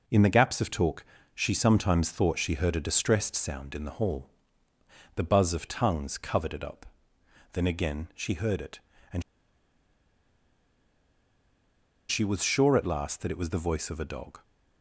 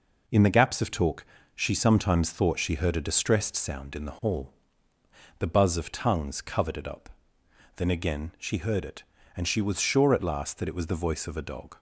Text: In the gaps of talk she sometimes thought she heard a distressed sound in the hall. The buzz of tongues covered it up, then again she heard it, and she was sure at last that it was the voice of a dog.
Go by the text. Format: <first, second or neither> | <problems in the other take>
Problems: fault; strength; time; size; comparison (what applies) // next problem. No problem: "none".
second | pauses between "talk" and "she"; slight; at 1.0 s; 0.30 s long; slight in the second // pauses between "and" and "she"; strong; at 9.2 s; 2.8 s long